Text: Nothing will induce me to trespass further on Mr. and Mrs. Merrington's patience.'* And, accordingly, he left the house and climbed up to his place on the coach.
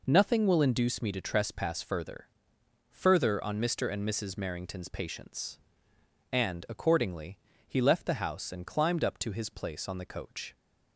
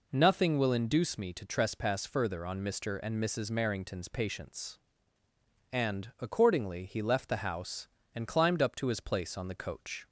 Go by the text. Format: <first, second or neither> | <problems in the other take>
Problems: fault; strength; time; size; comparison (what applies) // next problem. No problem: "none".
second | says "further" twice; at 2.9 s